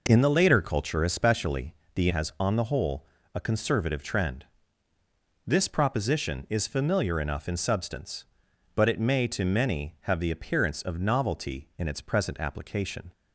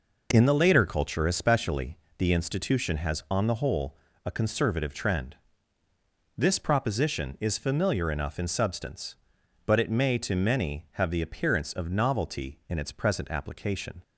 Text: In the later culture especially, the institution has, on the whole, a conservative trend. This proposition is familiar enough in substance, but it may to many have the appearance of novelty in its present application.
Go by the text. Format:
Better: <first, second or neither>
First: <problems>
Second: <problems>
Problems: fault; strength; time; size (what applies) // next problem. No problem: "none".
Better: second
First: skips "institution"; at 2.0 s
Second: none